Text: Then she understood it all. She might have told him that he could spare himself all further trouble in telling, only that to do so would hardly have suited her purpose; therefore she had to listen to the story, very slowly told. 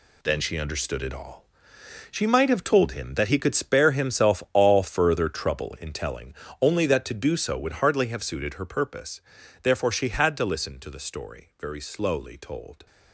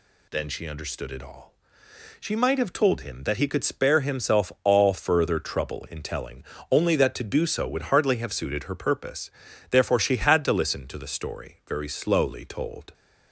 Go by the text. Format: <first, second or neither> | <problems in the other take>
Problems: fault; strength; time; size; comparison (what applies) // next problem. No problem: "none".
second | gets quieter; strong; throughout; 9.5 dB